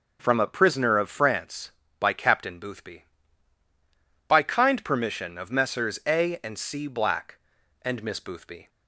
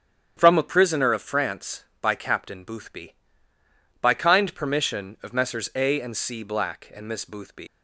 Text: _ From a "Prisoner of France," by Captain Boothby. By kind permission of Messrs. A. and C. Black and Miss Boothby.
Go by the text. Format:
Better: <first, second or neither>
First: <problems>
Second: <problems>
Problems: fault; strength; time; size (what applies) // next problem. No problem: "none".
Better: first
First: starts louder than the rest; noticeable; until 1.2 s; 6 dB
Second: starts louder than the rest; strong; until 1.3 s; 9 dB // leaves "Boothby" unfinished; at 7.6 s; 125 ms